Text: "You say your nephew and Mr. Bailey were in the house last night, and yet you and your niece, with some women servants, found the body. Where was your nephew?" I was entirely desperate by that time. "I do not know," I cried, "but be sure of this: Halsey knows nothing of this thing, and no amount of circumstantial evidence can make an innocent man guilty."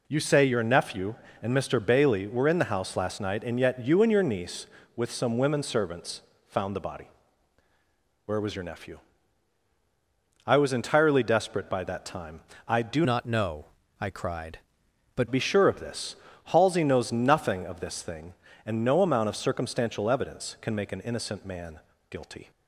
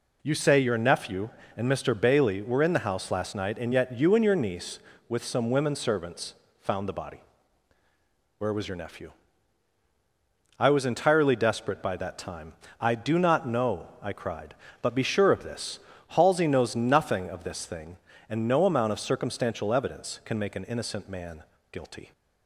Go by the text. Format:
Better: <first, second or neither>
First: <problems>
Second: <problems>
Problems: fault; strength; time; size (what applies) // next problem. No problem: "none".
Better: second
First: changes voice from "not" to "but"; from 13.0 to 15.2 s; 2.2 s long // pauses between "man" and "guilty"; slight; at 21.8 s; 0.30 s long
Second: pauses between "man" and "guilty"; slight; at 21.4 s; 0.28 s long